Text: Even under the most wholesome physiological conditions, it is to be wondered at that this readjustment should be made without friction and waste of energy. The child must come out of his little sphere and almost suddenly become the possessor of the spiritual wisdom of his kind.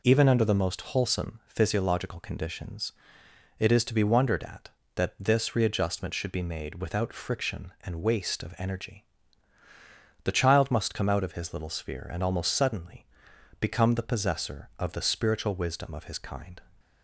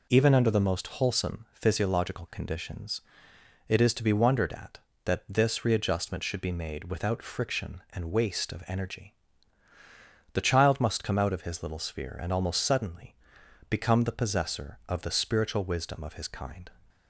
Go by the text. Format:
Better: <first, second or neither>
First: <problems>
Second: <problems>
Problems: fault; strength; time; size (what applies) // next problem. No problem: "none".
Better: neither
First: pauses between "suddenly" and "become"; noticeable; at 13.0 s; 0.54 s long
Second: pauses between "suddenly" and "become"; noticeable; at 13.1 s; 0.54 s long